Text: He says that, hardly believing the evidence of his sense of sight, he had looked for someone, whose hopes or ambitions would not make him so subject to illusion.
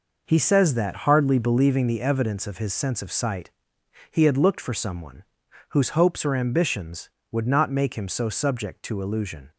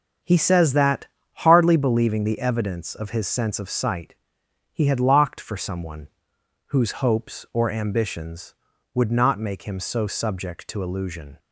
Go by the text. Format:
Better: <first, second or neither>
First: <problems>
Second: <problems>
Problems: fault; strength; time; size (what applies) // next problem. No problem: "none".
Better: first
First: none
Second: starts louder than the rest; until 1.5 s; 7 dB // says "locked" for "looked"; at 5.0 s